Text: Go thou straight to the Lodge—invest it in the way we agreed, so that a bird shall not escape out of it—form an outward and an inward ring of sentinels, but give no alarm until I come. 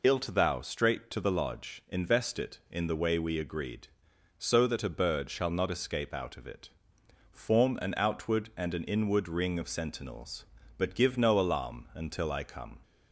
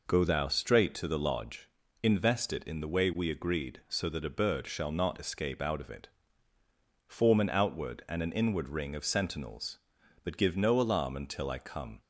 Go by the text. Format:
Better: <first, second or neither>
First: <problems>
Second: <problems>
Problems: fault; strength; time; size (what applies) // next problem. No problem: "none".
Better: second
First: says "Ilt" for "Go"; at 0.0 s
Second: none